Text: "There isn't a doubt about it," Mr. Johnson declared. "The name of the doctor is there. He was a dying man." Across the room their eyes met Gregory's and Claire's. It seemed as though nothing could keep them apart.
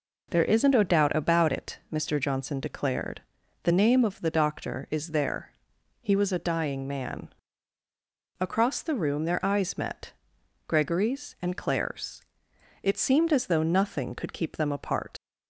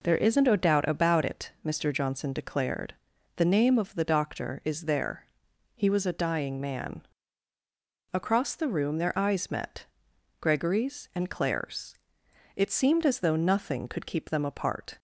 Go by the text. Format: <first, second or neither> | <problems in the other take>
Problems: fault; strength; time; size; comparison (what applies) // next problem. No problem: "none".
second | pauses between "met" and "Gregory's"; noticeable; at 10.1 s; 0.54 s long; noticeable in the second // leaves "apart" unfinished; at 15.1 s; 85 ms